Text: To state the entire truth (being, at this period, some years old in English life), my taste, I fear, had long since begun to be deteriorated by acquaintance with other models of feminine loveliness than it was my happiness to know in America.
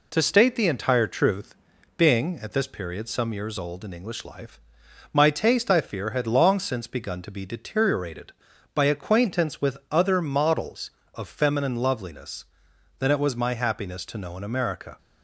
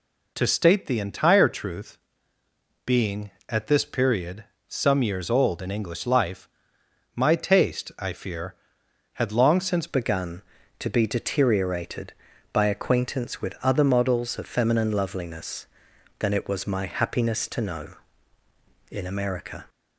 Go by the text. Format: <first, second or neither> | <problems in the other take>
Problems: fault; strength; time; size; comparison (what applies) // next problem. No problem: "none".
first | changes voice at "begun"; from 9.8 s on; 9.8 s long